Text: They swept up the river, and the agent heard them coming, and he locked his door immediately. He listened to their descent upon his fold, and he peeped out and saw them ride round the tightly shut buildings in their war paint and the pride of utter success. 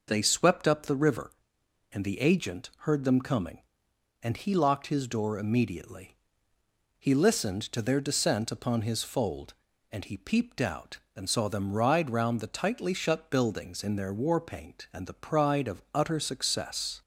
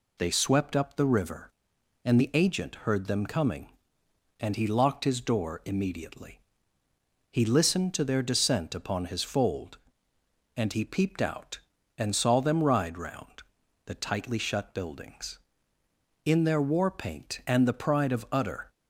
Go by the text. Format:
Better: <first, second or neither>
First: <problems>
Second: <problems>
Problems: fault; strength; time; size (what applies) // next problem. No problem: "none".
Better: first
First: none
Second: pauses between "round" and "the"; noticeable; at 13.2 s; 0.60 s long // stops before "success"; at 18.7 s